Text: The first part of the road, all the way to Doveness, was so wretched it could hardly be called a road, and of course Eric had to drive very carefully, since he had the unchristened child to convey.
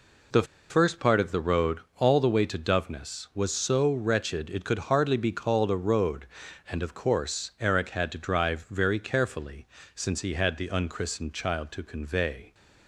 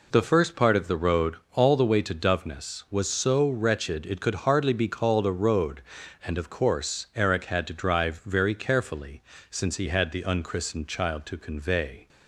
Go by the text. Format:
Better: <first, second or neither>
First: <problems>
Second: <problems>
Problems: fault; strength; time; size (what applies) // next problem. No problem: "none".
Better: second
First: pauses between "The" and "first"; slight; at 0.4 s; 0.25 s long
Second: none